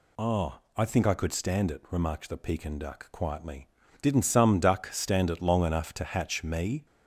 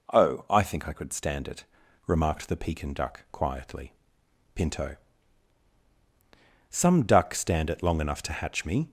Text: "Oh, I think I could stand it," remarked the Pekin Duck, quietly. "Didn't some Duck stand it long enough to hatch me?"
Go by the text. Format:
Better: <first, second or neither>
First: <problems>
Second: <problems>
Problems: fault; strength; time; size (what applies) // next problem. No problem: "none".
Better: first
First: none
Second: says "Pinto" for "Didn't"; at 4.5 s